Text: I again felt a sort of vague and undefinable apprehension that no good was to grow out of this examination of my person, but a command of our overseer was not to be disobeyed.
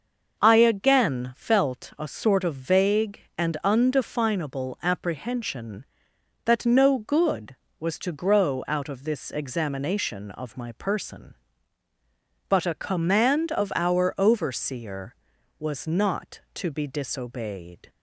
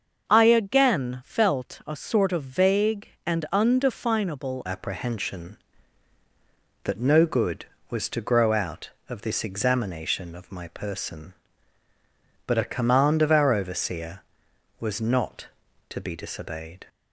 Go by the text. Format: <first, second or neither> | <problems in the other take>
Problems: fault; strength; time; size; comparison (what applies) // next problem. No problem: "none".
first | starts louder than the rest; until 1.3 s; 6.5 dB; noticeable in the first // changes voice at "apprehension"; from 4.6 s on; 12.2 s long